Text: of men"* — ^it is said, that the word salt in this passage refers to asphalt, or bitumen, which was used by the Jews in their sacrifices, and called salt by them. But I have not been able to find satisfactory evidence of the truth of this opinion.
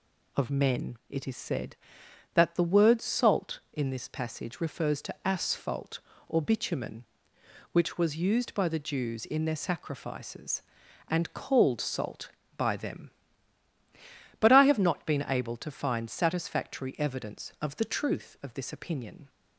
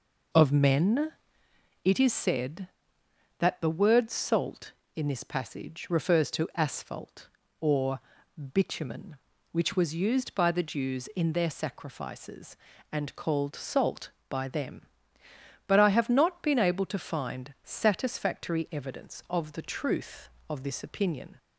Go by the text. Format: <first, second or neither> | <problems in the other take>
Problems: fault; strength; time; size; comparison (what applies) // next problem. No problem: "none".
first | starts louder than the rest; noticeable; until 1.7 s; 4.5 dB // pauses between "or" and "bitumen"; noticeable; at 7.9 s; 0.54 s long